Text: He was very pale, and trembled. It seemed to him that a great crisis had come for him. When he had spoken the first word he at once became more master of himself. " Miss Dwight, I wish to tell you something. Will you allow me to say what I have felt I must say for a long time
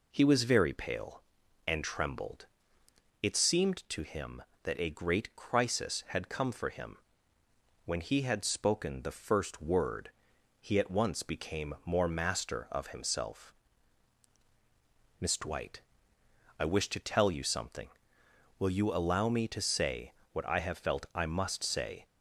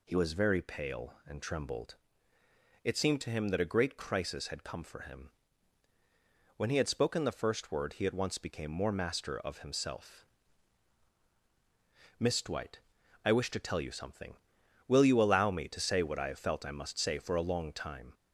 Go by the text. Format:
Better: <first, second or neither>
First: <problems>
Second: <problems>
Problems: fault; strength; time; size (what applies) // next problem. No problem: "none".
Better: second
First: pauses between "word" and "he"; noticeable; at 10.1 s; 0.52 s long // pauses between "say" and "what"; slight; at 20.1 s; 0.20 s long // stops before "for a long time"; at 22.0 s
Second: none